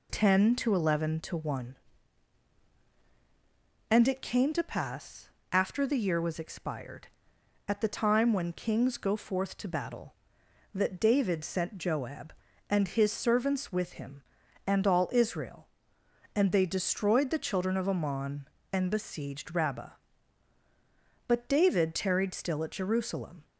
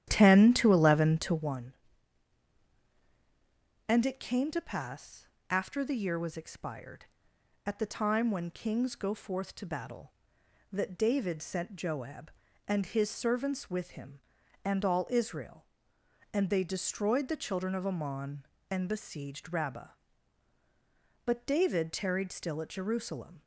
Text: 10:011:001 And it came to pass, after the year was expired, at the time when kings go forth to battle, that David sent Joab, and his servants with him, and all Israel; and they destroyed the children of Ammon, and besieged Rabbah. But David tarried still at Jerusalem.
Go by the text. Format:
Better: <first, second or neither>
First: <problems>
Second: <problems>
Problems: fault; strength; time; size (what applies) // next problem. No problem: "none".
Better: first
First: none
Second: starts louder than the rest; strong; until 1.5 s; 11 dB